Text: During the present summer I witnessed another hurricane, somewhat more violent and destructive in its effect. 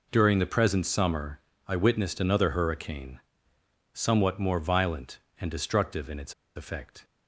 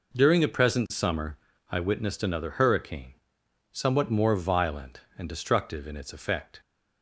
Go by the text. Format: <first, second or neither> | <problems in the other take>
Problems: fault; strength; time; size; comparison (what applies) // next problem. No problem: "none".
second | pauses between "summer" and "I"; slight; at 1.3 s; 0.28 s long; slight in the second // pauses between "its" and "effect"; slight; at 6.3 s; 0.22 s long